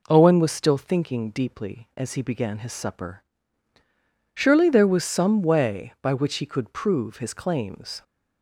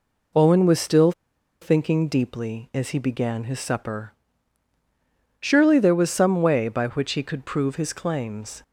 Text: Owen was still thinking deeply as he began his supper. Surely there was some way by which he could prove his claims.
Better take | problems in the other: first | pauses between "still" and "thinking"; noticeable; at 1.1 s; 0.50 s long

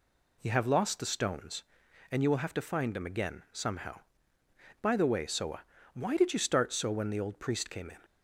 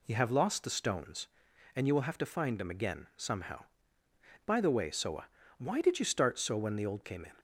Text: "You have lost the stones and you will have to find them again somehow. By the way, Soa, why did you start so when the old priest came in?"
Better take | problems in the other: first | skips "priest"; at 7.0 s

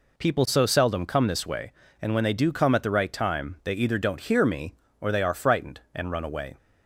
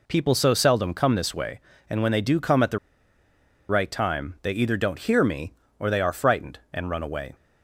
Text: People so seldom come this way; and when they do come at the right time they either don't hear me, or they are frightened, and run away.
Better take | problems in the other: first | pauses between "the" and "right"; noticeable; at 2.7 s; 0.91 s long

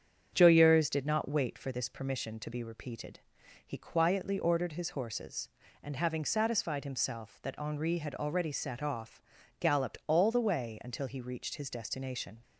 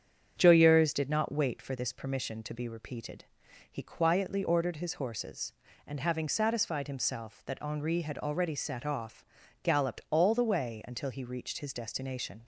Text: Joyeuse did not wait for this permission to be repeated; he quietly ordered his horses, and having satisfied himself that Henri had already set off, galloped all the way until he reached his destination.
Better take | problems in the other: neither | starts louder than the rest; strong; the same in both

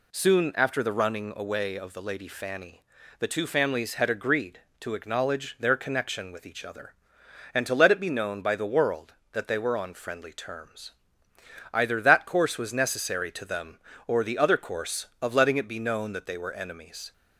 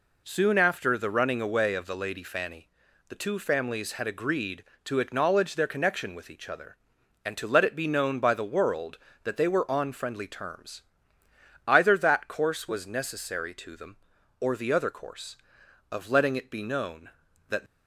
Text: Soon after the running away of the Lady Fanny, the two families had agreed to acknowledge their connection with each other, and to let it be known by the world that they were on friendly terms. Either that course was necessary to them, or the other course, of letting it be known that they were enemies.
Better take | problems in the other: first | stops before "they were enemies"; at 17.6 s

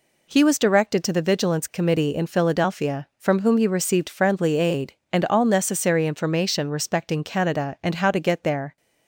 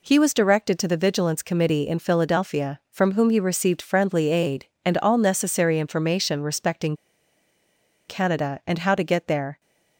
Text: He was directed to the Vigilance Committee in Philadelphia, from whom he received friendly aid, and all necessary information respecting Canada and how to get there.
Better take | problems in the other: first | pauses between "respecting" and "Canada"; at 6.9 s; 1.1 s long

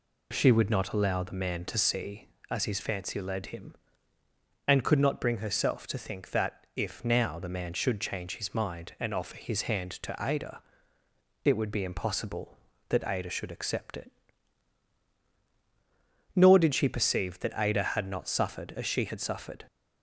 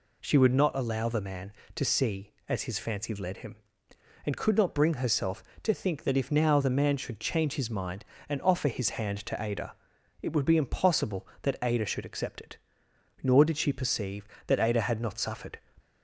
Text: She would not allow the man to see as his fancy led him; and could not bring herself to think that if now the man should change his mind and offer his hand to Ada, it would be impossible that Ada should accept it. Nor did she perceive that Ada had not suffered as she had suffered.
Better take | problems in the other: first | stops before "as she had suffered"; at 15.7 s

